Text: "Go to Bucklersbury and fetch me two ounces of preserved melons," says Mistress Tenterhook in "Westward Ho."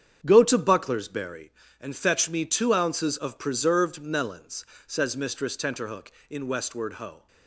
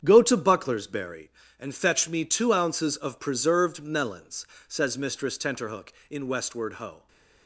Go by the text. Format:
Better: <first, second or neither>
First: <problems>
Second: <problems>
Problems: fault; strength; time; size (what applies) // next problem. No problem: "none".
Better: neither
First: starts louder than the rest; strong; until 1.2 s; 8 dB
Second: starts louder than the rest; strong; until 1.0 s; 8 dB